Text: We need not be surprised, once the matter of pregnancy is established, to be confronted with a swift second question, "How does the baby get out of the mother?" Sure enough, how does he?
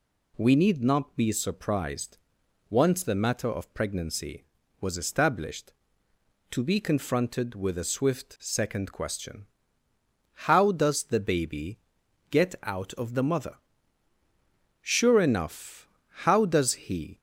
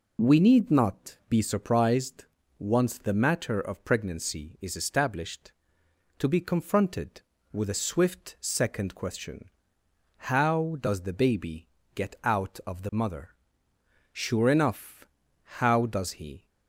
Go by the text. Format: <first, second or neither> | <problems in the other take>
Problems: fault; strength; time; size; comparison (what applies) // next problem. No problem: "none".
second | says "was" for "is"; at 4.8 s // pauses between "baby" and "get"; noticeable; at 11.7 s; 0.52 s long; slight in the second